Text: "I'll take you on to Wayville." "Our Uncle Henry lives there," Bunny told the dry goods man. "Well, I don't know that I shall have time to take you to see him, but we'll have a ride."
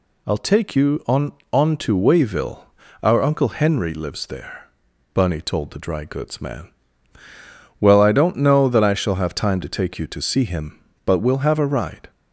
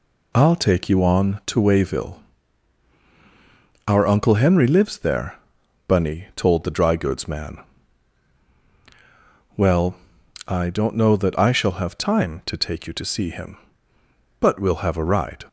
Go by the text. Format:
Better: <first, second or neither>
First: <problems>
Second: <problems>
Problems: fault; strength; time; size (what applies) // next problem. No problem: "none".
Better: second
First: says "on" twice; at 1.5 s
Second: none